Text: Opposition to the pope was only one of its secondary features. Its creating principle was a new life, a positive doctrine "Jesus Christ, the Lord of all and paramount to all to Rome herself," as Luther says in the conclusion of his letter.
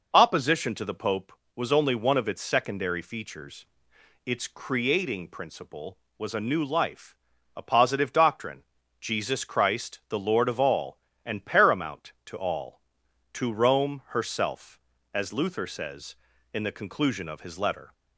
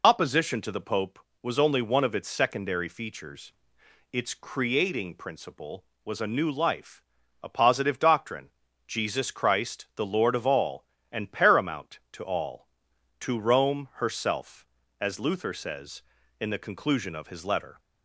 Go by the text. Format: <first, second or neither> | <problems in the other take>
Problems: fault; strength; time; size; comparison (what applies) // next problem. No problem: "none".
first | loses the start of "Opposition"; at 0.0 s; 45 ms // pauses between "doctrine" and "Jesus"; at 8.4 s; 0.38 s long; also in the first